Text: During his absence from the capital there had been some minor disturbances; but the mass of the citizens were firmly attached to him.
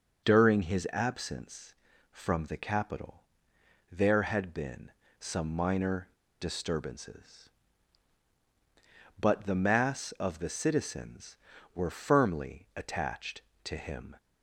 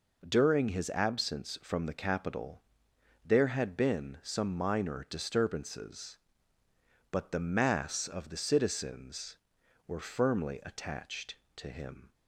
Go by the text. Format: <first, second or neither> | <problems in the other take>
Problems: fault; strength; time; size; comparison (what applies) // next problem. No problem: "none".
second | starts louder than the rest; noticeable; until 1.2 s; 6 dB // pauses between "capital" and "there"; noticeable; at 3.2 s; 0.68 s long; noticeable in the second // pauses between "been" and "some"; slight; at 4.9 s; 0.28 s long // pauses between "minor" and "disturbances"; slight; at 6.0 s; 0.32 s long